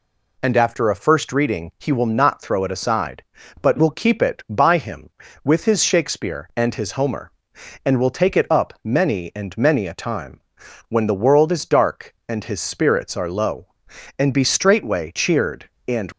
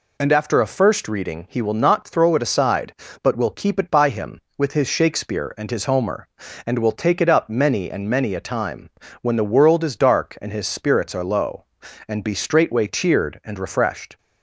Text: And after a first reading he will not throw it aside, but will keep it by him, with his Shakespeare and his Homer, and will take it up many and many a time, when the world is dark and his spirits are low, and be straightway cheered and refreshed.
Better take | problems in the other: second | stops before "refreshed"; at 16.1 s

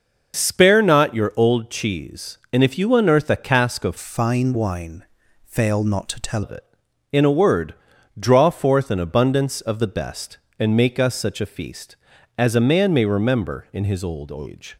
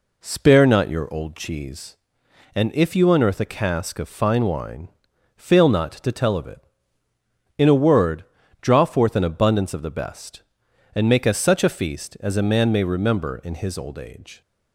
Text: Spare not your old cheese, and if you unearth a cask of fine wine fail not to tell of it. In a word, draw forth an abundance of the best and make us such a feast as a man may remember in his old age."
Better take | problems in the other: second | starts louder than the rest; noticeable; until 1.4 s; 6 dB // changes voice from "fine" to "tell"; from 3.9 to 6.4 s; 2.5 s long // pauses between "wine" and "fail"; at 5.0 s; 0.40 s long; noticeable in the second

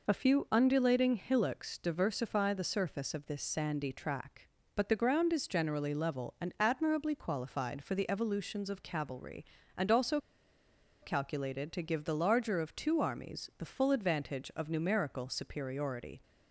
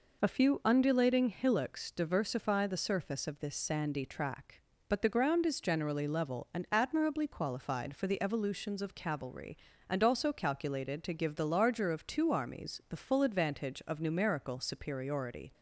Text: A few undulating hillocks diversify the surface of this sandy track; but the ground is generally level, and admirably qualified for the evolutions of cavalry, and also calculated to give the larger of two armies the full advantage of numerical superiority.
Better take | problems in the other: second | pauses between "also" and "calculated"; noticeable; at 10.2 s; 0.81 s long

